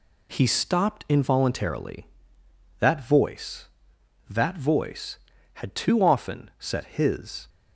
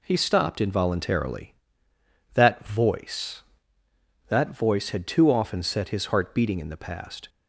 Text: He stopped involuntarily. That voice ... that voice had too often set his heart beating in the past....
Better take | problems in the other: second | stops before "heart beating in the past"; at 7.4 s

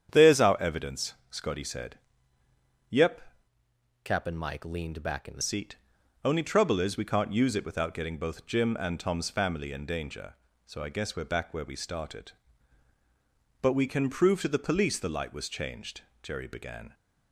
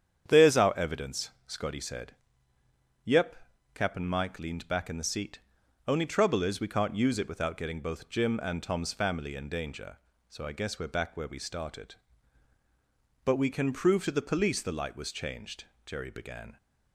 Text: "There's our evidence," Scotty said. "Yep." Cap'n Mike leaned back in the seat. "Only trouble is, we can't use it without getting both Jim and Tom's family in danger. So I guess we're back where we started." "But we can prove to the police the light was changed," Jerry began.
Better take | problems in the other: second | starts louder than the rest; strong; until 1.1 s; 8.5 dB; strong in the second // changes voice from "Cap'n" to "the"; from 4.0 to 5.4 s; 1.4 s long

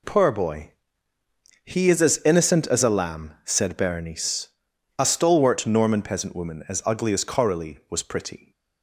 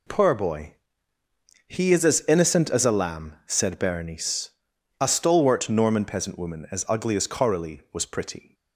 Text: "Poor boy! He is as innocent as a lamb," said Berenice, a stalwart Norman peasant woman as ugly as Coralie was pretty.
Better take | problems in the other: neither | none

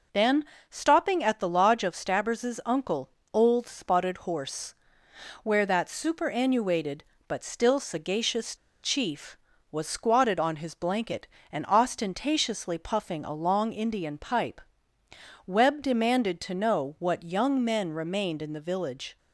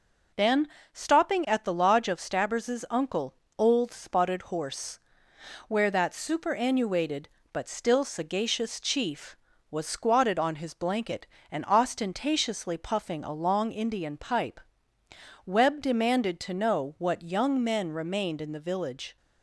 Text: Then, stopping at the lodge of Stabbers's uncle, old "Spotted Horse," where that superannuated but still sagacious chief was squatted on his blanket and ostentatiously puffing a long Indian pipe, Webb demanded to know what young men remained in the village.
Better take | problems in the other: second | pauses between "sagacious" and "chief"; slight; at 8.5 s; 0.27 s long

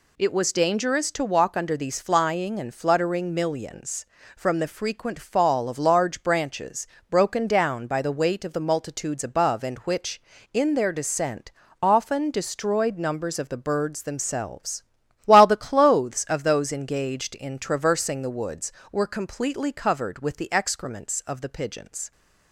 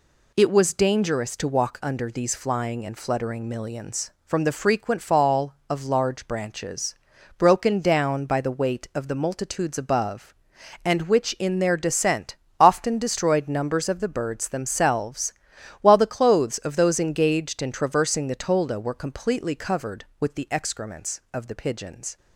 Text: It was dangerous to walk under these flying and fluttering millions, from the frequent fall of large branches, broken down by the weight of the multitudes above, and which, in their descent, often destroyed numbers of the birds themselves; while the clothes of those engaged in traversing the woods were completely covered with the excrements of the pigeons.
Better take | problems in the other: first | says "tolda" for "woods"; at 18.3 s

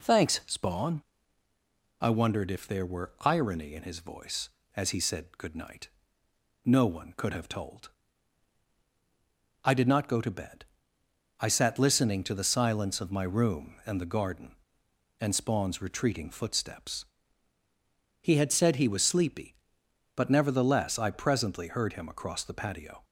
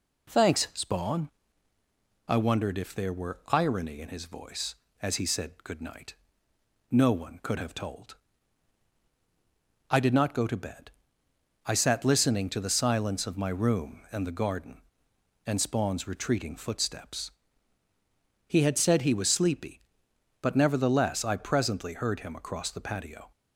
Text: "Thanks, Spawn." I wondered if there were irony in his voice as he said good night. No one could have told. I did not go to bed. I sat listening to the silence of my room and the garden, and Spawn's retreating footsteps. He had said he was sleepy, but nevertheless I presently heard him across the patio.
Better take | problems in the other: neither | none

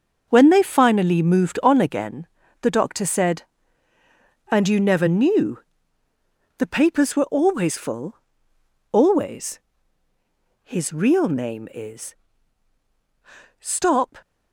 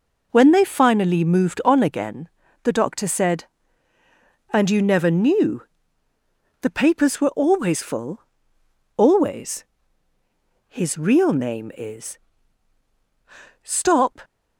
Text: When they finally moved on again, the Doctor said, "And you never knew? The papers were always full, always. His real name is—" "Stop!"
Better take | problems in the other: second | gets quieter; strong; throughout; 9.5 dB

